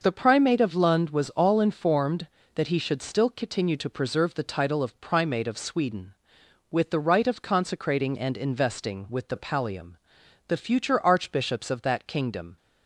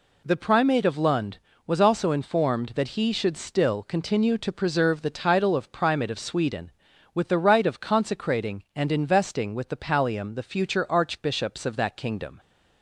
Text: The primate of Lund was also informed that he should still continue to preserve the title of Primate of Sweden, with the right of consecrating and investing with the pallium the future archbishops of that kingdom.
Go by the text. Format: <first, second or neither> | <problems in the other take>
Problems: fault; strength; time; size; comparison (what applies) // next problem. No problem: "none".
second | says "all" for "also"; at 1.2 s // pauses between "pallium" and "the"; noticeable; at 9.9 s; 0.52 s long